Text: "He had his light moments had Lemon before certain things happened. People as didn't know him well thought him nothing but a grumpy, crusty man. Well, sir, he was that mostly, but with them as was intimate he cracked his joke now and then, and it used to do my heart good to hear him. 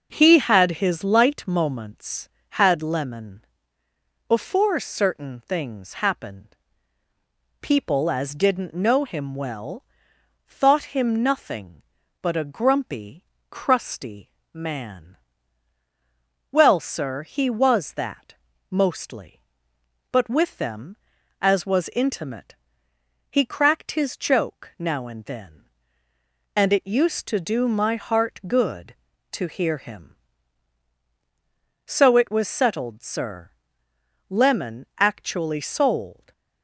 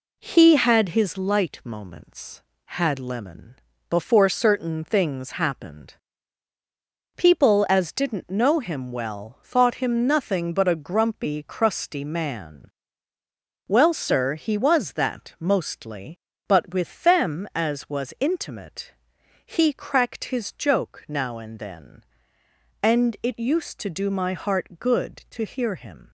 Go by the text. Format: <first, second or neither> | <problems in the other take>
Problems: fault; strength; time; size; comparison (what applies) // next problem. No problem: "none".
second | pauses between "Lemon" and "before"; noticeable; at 3.4 s; 0.82 s long; slight in the second // pauses between "well" and "thought"; noticeable; at 9.8 s; 0.62 s long // pauses between "crusty" and "man"; slight; at 14.3 s; 0.20 s long // pauses between "that" and "mostly"; slight; at 18.3 s; 0.34 s long // pauses between "intimate" and "he"; noticeable; at 22.5 s; 0.74 s long; noticeable in the second // goes on to say "So it was settled sir Lemon actually sold"; strong; from 31.8 s on; 4.4 s long // stays silent after the last word; slight; from 36.1 s on; 0.5 s long